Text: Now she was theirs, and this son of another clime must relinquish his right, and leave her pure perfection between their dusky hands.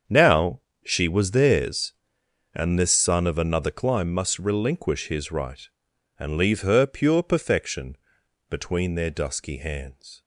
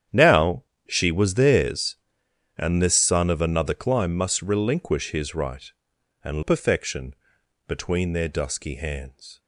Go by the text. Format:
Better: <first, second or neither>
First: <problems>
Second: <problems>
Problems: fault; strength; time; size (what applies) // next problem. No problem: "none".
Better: first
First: starts louder than the rest; strong; until 1.3 s; 7 dB // pauses between "Now" and "she"; slight; at 0.5 s; 0.24 s long // pauses between "perfection" and "between"; noticeable; at 7.9 s; 0.54 s long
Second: starts louder than the rest; strong; until 1.3 s; 9.5 dB // pauses between "Now" and "she"; slight; at 0.6 s; 0.24 s long // skips "leave her pure"; at 6.4 s // pauses between "perfection" and "between"; noticeable; at 7.1 s; 0.54 s long